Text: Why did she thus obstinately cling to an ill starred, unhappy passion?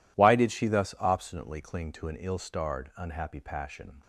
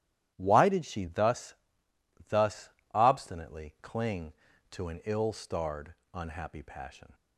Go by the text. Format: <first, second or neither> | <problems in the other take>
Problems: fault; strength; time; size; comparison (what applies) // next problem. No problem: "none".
first | starts louder than the rest; strong; until 1.4 s; 12 dB // says "thus" twice; at 2.2 s